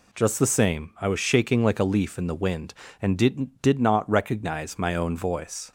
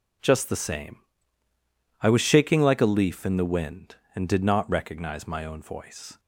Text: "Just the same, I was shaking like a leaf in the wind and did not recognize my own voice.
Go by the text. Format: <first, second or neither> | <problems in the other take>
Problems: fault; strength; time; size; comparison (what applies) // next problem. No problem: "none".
second | says "did" twice; at 3.6 s